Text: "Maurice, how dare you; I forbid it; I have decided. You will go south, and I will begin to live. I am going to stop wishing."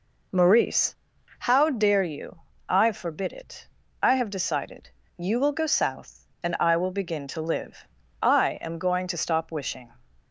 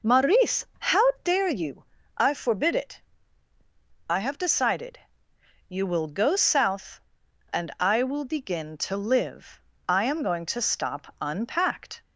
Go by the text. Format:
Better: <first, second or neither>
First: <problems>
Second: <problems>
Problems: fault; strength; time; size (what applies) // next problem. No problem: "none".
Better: first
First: none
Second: says "unpacked" for "wishing"; at 11.2 s